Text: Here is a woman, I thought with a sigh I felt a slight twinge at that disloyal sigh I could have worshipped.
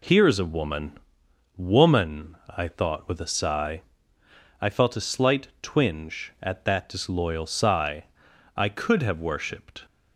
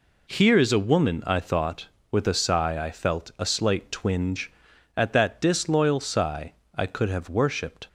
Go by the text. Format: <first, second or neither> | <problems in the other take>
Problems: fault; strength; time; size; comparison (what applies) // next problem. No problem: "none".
second | says "woman" twice; at 1.5 s // pauses between "sigh" and "I"; noticeable; at 3.8 s; 0.76 s long // pauses between "sigh" and "I"; noticeable; at 8.0 s; 0.54 s long; slight in the second